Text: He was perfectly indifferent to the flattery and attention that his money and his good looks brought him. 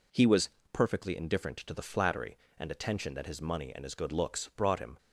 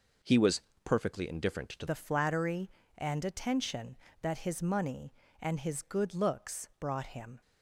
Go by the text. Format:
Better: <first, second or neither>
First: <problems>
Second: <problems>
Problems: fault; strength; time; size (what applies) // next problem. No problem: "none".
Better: first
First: pauses between "was" and "perfectly"; slight; at 0.4 s; 0.22 s long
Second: pauses between "was" and "perfectly"; slight; at 0.6 s; 0.22 s long // changes voice at "the"; from 1.8 s on; 5.6 s long